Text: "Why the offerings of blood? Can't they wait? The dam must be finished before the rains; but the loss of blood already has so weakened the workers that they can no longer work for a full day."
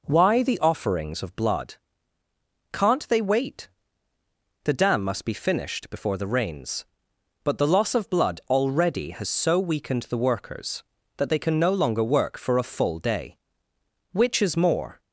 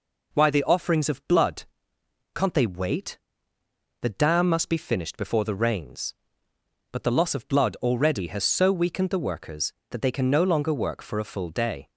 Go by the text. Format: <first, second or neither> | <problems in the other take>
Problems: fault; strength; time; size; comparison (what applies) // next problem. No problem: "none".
second | goes on to say "Which is more"; noticeable; from 14.1 s on; 0.90 s long